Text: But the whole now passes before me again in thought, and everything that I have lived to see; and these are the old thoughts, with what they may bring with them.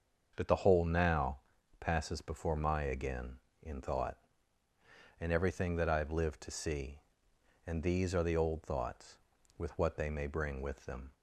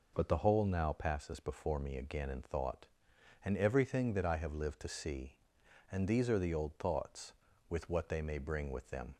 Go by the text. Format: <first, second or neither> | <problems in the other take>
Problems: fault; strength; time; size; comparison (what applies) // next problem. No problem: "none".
second | starts louder than the rest; until 1.3 s; 6.5 dB // pauses between "now" and "passes"; at 1.3 s; 0.40 s long // says "my" for "me"; at 2.5 s